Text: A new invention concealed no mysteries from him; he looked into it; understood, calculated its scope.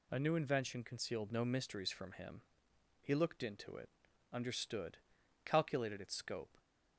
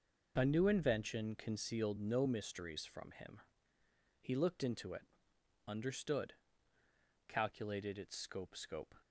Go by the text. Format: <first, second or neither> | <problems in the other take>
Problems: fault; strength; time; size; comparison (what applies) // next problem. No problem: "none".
first | says "scope" twice; at 8.5 s